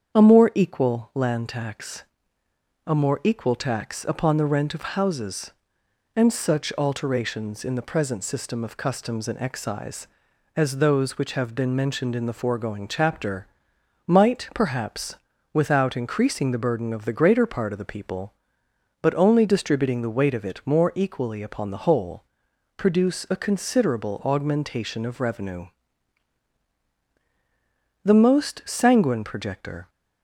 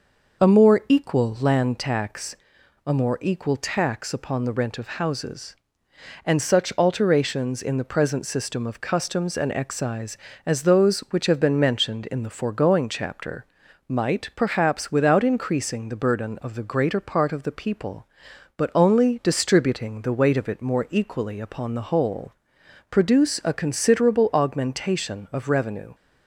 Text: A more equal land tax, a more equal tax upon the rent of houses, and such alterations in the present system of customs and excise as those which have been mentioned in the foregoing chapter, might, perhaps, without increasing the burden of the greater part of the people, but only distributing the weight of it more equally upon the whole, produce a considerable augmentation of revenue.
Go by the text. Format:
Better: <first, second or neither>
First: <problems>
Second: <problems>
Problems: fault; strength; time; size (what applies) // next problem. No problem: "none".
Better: second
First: starts louder than the rest; strong; until 1.2 s; 7.5 dB // goes on to say "The most sanguine projector"; strong; from 28.0 s on; 1.8 s long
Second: none